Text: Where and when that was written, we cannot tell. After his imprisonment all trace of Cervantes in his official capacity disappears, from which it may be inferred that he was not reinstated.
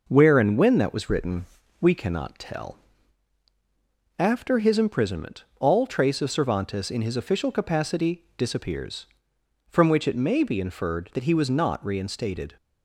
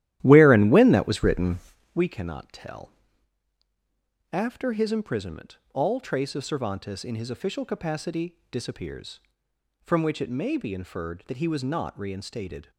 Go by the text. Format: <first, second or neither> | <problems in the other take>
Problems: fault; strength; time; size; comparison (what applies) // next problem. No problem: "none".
first | starts louder than the rest; strong; until 2.0 s; 13.5 dB // pauses between "imprisonment" and "all"; slight; at 5.5 s; 0.16 s long; slight in the first